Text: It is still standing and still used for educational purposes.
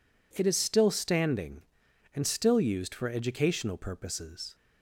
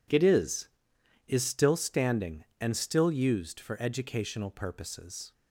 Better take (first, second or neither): first